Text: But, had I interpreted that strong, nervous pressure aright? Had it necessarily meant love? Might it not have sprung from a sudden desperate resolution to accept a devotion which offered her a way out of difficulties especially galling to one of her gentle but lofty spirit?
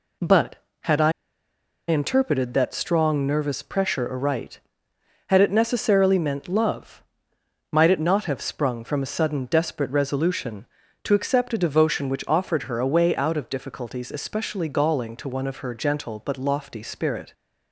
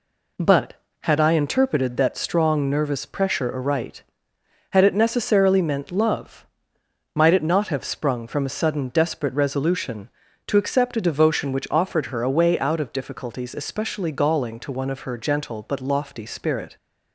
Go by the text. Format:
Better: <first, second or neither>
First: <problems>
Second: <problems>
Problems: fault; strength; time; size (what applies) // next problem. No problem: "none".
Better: second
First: pauses between "I" and "interpreted"; noticeable; at 1.1 s; 0.77 s long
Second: none